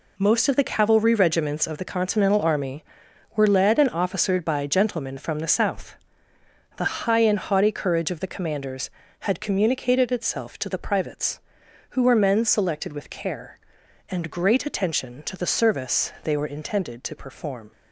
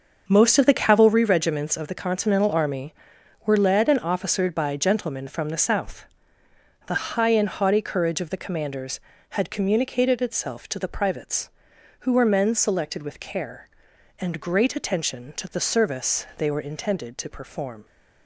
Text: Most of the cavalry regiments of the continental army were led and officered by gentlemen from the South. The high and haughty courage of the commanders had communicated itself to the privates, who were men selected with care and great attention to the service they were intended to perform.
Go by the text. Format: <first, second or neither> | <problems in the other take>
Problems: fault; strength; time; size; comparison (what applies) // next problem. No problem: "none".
first | starts louder than the rest; until 1.2 s; 6.5 dB